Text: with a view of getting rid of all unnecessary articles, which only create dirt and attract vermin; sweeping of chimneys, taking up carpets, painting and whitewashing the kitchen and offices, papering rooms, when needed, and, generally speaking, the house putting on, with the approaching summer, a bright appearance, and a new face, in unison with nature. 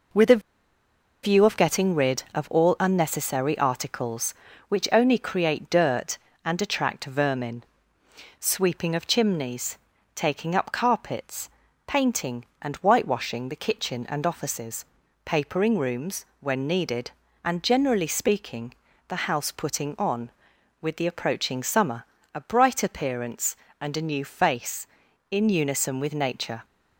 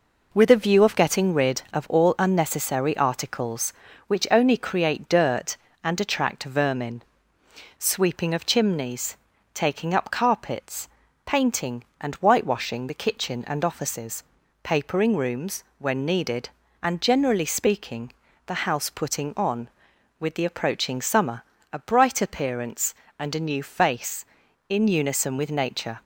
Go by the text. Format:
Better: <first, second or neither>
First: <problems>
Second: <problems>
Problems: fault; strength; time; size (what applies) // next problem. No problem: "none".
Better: second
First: pauses between "a" and "view"; noticeable; at 0.4 s; 0.82 s long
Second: none